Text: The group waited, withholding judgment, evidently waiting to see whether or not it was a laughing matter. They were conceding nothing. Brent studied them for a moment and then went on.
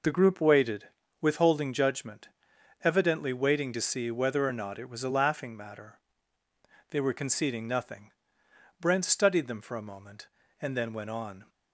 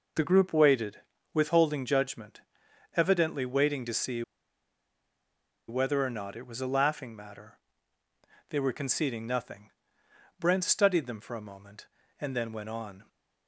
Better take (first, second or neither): first